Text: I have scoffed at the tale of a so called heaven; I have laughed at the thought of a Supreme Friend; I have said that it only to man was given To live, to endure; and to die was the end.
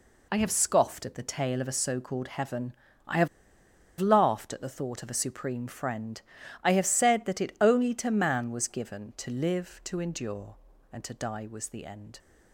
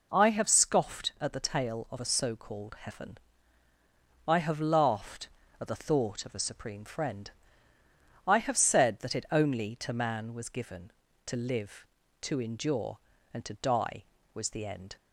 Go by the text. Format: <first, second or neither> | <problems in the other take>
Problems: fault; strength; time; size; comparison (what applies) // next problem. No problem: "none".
second | pauses between "have" and "laughed"; noticeable; at 3.2 s; 0.72 s long